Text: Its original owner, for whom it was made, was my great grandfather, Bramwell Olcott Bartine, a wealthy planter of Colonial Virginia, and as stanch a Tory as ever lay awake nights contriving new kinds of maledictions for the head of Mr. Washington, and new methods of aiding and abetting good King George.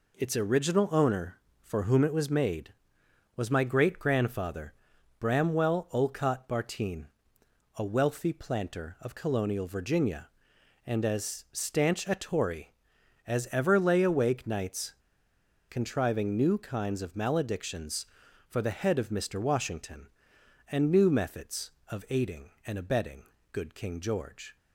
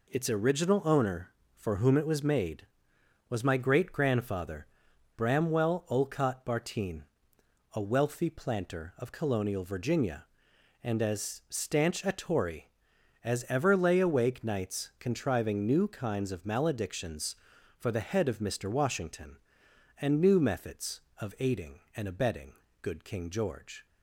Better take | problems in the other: second | pauses between "nights" and "contriving"; noticeable; at 14.9 s; 0.77 s long // pauses between "abetting" and "good"; slight; at 23.2 s; 0.28 s long; slight in the second

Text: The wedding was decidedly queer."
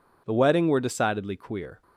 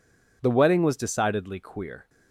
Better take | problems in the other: second | says "were" for "was"; at 0.6 s

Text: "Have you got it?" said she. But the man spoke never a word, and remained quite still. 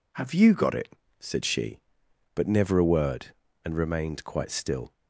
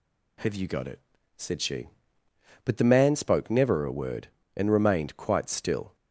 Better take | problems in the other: second | skips "the man spoke"; at 2.4 s

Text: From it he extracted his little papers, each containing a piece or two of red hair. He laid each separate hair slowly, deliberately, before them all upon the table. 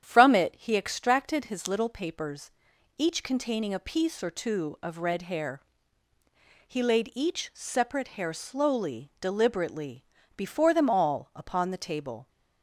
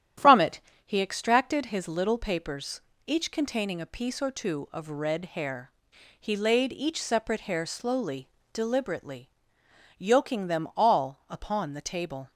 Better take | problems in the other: first | starts louder than the rest; strong; until 1.4 s; 10 dB; strong in the first // pauses between "it" and "he"; slight; at 0.5 s; 0.26 s long // says "yoking" for "before"; at 9.9 s

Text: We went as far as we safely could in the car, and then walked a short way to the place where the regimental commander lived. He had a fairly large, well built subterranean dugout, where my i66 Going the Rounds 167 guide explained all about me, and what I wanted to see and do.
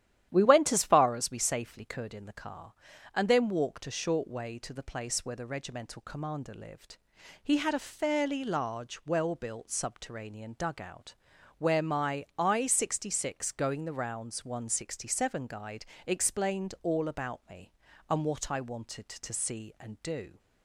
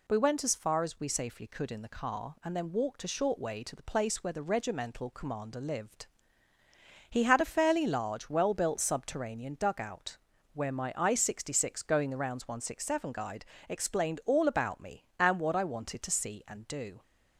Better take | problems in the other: second | starts louder than the rest; strong; until 2.0 s; 11.5 dB // pauses between "guide" and "explained"; slight; at 15.8 s; 0.20 s long; slight in the second

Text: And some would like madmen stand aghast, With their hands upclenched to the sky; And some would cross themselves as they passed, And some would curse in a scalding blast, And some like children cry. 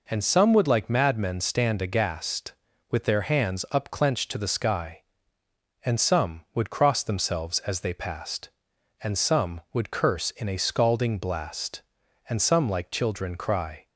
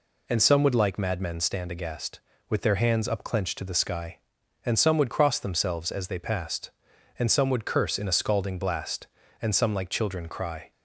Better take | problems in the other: neither | none

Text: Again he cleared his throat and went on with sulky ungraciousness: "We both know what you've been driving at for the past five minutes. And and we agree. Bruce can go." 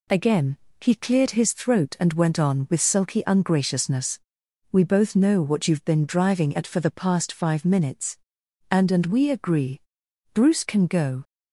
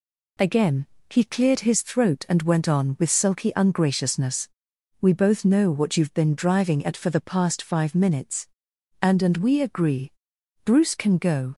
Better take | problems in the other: neither | pauses between "Again" and "he"; slight; the same in both

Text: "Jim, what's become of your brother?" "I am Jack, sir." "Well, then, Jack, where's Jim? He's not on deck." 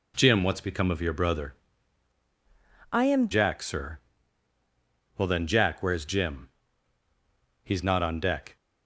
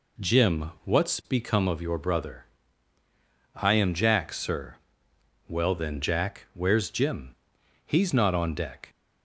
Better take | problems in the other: second | changes voice from "I" to "am"; from 2.9 to 3.2 s; 0.3 s long

